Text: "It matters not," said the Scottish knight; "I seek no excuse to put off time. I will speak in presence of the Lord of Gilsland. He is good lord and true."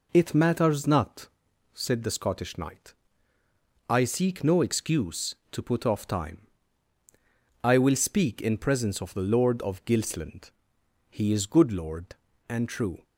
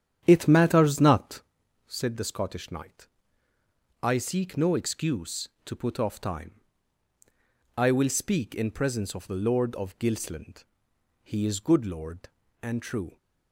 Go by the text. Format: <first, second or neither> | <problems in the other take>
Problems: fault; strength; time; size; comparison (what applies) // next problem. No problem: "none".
first | starts louder than the rest; strong; until 1.5 s; 9.5 dB